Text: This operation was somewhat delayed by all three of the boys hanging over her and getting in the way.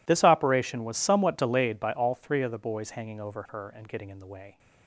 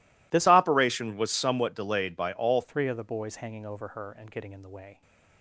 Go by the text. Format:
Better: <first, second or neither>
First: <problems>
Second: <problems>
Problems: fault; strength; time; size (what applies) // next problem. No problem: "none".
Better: first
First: none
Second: changes voice from "operation" to "all"; from 0.4 to 2.6 s; 2.2 s long